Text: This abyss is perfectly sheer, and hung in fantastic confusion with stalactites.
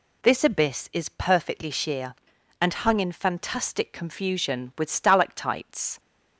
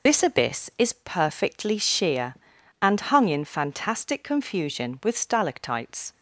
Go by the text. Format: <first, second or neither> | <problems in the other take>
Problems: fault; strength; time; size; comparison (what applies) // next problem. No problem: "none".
first | loses the start of "This"; at 0.0 s; 75 ms